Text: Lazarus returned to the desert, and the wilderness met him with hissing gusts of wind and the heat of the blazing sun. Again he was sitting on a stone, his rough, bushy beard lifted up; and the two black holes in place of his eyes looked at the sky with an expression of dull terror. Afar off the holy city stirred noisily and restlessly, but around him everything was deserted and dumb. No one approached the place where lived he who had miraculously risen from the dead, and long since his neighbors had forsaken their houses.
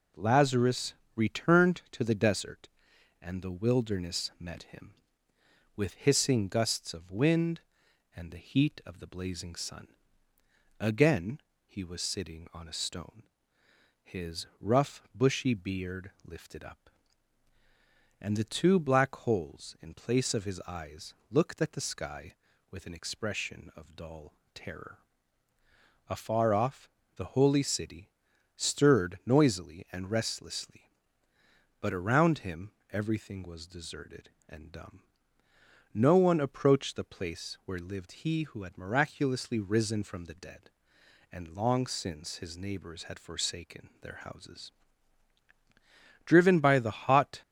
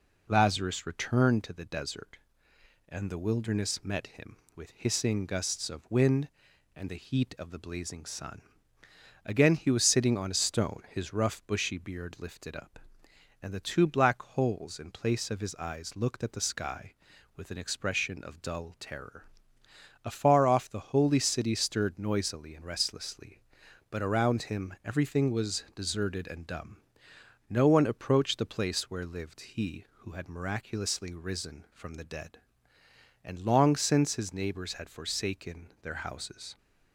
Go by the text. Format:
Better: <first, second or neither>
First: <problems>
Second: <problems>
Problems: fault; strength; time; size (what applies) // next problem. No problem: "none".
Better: second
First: pauses between "Lazarus" and "returned"; slight; at 0.9 s; 0.22 s long // pauses between "Again" and "he"; slight; at 11.3 s; 0.26 s long // pauses between "eyes" and "looked"; slight; at 21.1 s; 0.16 s long // pauses between "dull" and "terror"; slight; at 24.3 s; 0.20 s long // pauses between "off" and "the"; slight; at 26.8 s; 0.26 s long // pauses between "city" and "stirred"; noticeable; at 28.0 s; 0.48 s long // pauses between "him" and "everything"; slight; at 32.7 s; 0.20 s long // goes on to say "Driven by the hot"; noticeable; from 46.2 s on; 1.1 s long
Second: none